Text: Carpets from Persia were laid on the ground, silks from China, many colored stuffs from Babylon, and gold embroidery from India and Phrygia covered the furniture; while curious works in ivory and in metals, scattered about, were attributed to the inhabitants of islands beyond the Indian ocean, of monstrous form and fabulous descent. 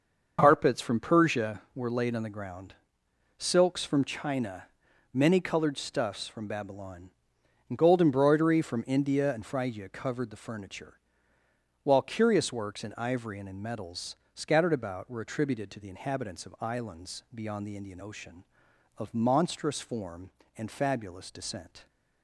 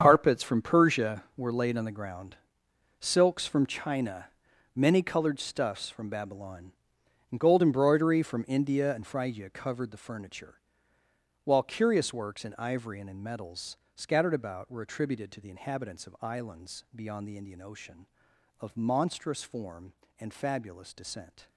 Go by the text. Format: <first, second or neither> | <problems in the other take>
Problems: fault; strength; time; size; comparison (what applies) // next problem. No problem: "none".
first | gets quieter; strong; throughout; 14 dB // starts louder than the rest; strong; until 1.0 s; 7.5 dB; also in the first